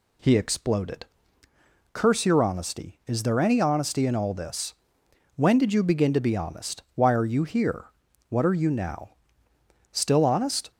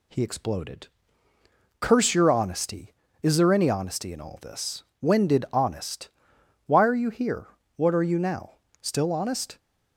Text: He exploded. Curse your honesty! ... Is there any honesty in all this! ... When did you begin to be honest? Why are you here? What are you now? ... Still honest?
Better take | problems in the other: first | skips "you begin to be"; at 5.4 s

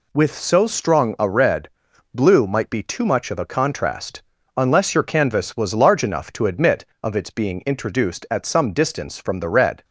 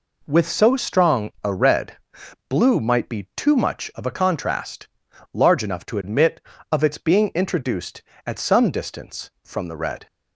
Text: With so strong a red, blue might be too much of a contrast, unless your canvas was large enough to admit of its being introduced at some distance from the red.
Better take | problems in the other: first | skips "unless your canvas was"; at 5.0 s

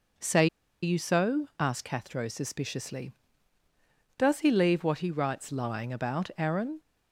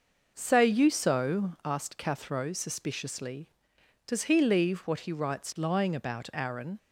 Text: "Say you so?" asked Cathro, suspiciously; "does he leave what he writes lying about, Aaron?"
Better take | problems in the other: second | pauses between "Say" and "you"; at 0.4 s; 0.36 s long

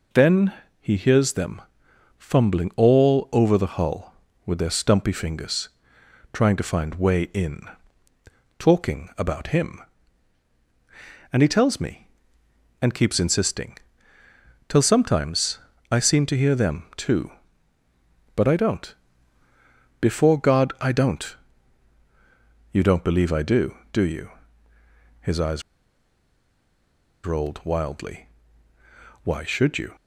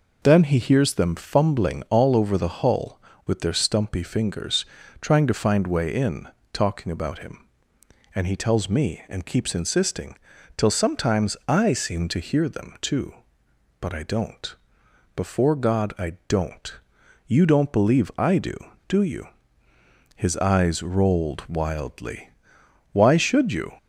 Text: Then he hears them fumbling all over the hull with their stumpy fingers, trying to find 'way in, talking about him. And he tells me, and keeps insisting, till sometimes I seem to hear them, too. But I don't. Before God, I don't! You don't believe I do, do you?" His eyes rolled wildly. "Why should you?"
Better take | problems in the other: second | pauses between "Then" and "he"; slight; at 0.5 s; 0.28 s long // pauses between "them" and "fumbling"; noticeable; at 1.6 s; 0.58 s long // pauses between "sometimes" and "I"; slight; at 15.5 s; 0.32 s long // pauses between "eyes" and "rolled"; strong; at 25.6 s; 1.6 s long

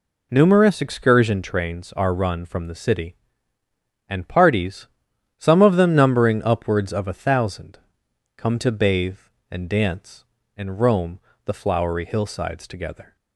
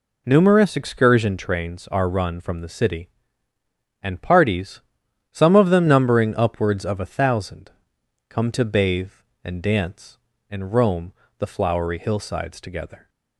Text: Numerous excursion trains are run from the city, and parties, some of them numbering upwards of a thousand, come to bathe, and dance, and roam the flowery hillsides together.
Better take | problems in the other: neither | pauses between "roam" and "the"; slight; the same in both

